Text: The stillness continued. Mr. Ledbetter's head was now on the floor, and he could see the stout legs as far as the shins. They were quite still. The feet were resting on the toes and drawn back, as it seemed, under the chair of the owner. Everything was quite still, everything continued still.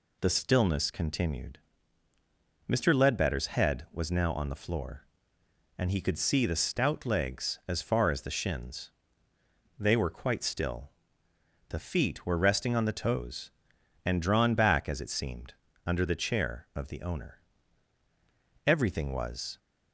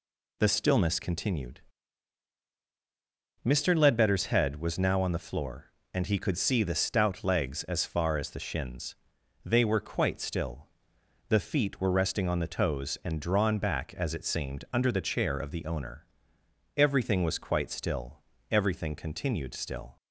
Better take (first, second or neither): second